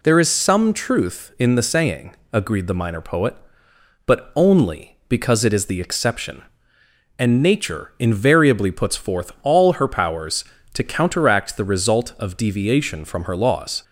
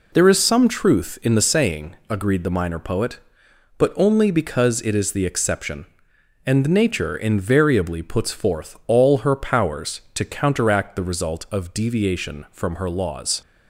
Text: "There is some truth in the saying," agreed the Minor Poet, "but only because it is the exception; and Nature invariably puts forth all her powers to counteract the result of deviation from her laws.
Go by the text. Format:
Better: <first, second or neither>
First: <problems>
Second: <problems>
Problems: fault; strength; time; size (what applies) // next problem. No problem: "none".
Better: neither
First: none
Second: none